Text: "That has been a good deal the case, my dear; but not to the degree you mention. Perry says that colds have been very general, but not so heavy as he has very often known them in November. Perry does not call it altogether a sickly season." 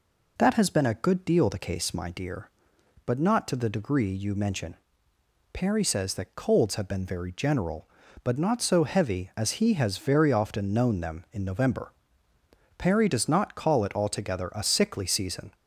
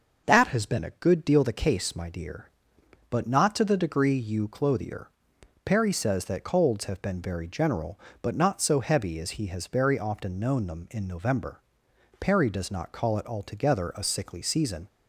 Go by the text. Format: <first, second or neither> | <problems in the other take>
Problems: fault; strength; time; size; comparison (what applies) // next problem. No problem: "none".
first | starts louder than the rest; until 1.2 s; 6 dB // says "clothier" for "mention"; at 4.4 s